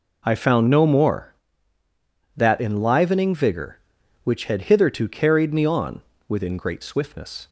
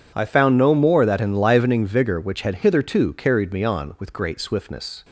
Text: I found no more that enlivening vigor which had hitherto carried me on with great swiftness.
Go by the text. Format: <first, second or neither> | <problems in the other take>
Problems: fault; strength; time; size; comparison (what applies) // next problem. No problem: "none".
second | says "within" for "with"; at 6.2 s